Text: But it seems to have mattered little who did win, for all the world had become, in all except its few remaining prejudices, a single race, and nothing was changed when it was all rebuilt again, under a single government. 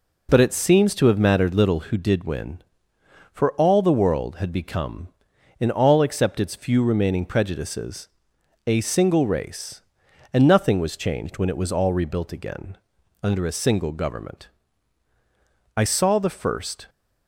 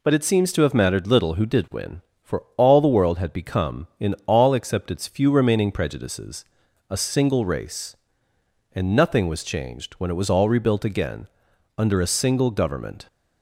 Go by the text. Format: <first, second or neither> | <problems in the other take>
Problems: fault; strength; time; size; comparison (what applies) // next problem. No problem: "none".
second | goes on to say "I saw the first"; noticeable; from 15.7 s on; 1.1 s long